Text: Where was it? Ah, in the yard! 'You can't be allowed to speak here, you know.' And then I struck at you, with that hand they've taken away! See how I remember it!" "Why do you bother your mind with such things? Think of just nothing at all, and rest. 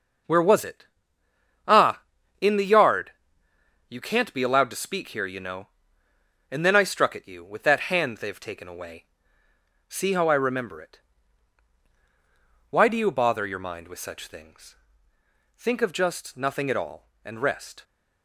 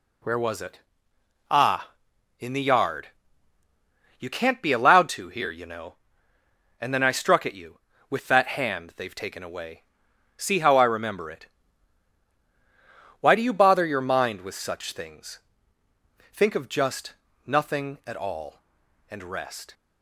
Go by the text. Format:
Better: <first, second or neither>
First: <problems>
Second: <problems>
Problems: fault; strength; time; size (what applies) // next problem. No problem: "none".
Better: first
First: none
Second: skips "speak"; at 5.2 s // pauses between "just" and "nothing"; slight; at 17.1 s; 0.34 s long